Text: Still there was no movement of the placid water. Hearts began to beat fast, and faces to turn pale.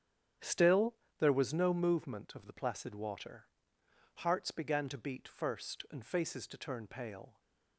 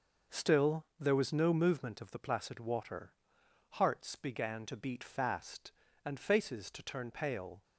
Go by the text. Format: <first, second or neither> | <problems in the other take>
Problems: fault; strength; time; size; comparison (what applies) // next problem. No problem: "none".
second | starts louder than the rest; strong; until 1.6 s; 9.5 dB // pauses between "Still" and "there"; slight; at 0.9 s; 0.24 s long // says "first" for "fast"; at 5.2 s